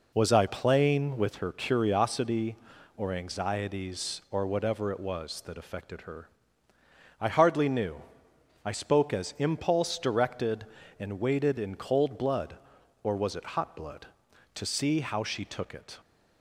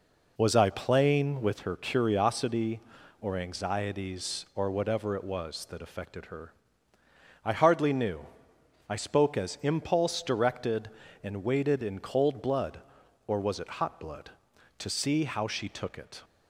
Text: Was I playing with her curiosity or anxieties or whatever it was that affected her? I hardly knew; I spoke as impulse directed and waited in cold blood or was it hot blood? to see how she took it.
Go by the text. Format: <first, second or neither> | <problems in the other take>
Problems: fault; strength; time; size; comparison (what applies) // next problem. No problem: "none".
neither | none